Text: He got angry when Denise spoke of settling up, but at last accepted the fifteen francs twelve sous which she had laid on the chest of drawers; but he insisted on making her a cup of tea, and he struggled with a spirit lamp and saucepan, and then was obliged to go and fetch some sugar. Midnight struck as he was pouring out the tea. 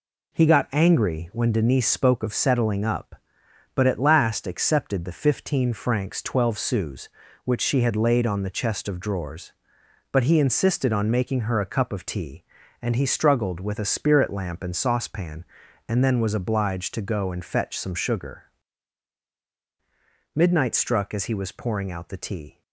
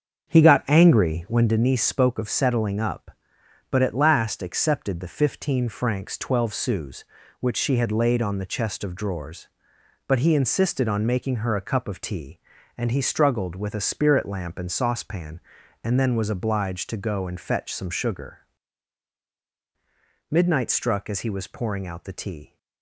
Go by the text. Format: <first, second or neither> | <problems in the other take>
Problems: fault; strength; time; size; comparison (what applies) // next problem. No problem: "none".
first | starts louder than the rest; until 1.6 s; 7 dB